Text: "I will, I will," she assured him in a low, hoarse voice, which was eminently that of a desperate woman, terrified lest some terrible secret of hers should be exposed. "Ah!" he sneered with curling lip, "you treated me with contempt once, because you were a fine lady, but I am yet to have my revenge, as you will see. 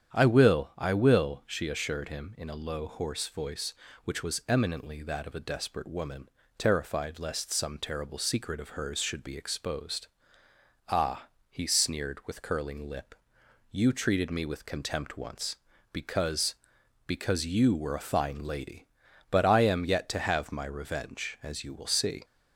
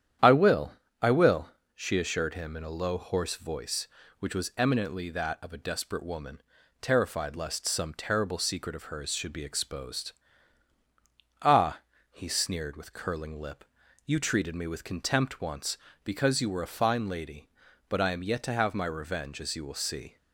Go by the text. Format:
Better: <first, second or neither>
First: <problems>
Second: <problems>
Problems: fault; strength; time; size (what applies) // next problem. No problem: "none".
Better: second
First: starts louder than the rest; strong; until 1.2 s; 9 dB // says "because" twice; at 17.0 s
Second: starts louder than the rest; strong; until 1.4 s; 10 dB